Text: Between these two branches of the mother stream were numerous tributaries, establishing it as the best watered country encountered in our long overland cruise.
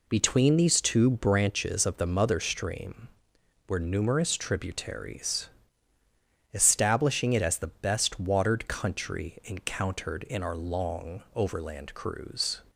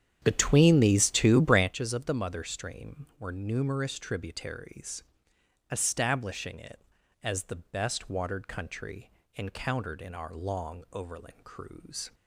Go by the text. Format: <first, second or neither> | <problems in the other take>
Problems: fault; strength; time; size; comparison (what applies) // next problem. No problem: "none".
first | starts louder than the rest; strong; until 1.7 s; 9 dB // pauses between "country" and "encountered"; slight; at 9.1 s; 0.24 s long